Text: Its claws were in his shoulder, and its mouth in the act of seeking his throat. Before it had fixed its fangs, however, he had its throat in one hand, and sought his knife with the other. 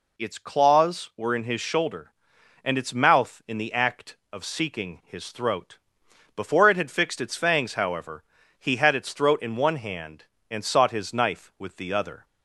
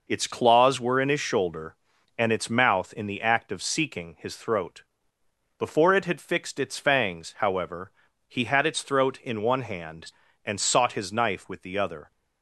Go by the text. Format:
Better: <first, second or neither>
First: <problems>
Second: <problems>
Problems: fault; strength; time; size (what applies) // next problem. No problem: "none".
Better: neither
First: none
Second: none